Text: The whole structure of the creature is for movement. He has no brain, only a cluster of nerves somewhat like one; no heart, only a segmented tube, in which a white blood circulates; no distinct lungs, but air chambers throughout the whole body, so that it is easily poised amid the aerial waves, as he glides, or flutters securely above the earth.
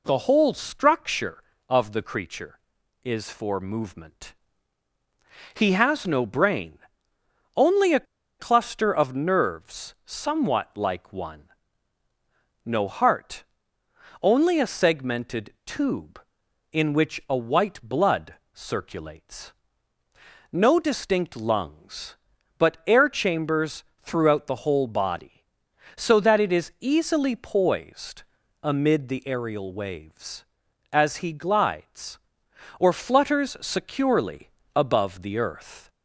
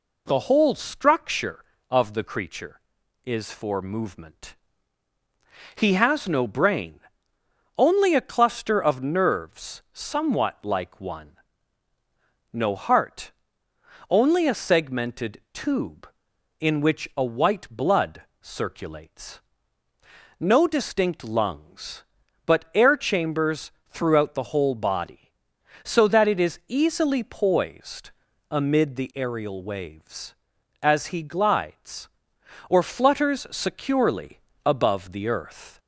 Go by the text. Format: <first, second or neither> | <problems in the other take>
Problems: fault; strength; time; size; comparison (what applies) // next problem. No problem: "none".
second | pauses between "a" and "cluster"; slight; at 8.0 s; 0.33 s long // pauses between "blood" and "circulates"; slight; at 18.3 s; 0.18 s long; slight in the second // pauses between "chambers" and "throughout"; slight; at 23.8 s; 0.16 s long; slight in the second // pauses between "poised" and "amid"; at 28.2 s; 0.38 s long; also in the second // pauses between "securely" and "above"; slight; at 34.4 s; 0.26 s long; slight in the second